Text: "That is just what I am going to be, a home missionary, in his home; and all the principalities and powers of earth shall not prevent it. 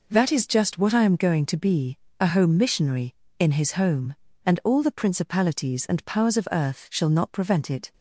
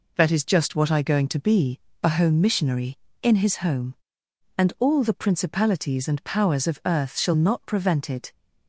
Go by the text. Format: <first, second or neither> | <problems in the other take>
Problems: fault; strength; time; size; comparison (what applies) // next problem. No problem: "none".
first | skips "am"; at 1.0 s